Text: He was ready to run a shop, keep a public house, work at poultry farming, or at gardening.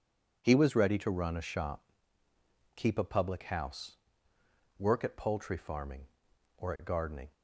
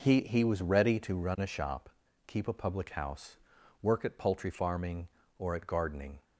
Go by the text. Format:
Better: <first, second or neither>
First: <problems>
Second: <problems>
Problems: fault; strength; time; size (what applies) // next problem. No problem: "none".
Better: first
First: none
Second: says "He" twice; at 0.2 s